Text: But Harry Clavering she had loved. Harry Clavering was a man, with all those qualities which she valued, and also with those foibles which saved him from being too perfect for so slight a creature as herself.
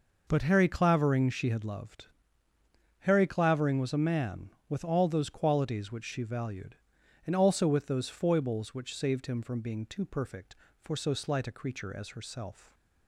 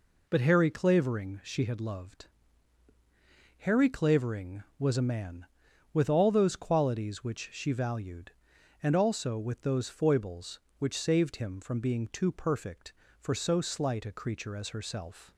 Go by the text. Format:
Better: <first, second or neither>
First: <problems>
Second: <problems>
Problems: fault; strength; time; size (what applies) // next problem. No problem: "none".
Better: neither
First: none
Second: none